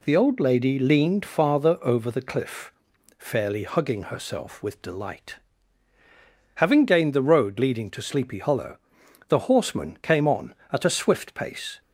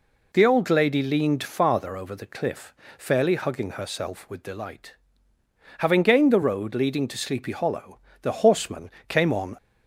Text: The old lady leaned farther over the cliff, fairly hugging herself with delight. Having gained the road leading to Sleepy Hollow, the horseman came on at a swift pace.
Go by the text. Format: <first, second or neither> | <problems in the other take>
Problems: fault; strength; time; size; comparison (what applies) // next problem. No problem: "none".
first | pauses between "horseman" and "came"; slight; at 8.9 s; 0.16 s long // stops before "at a swift pace"; at 9.5 s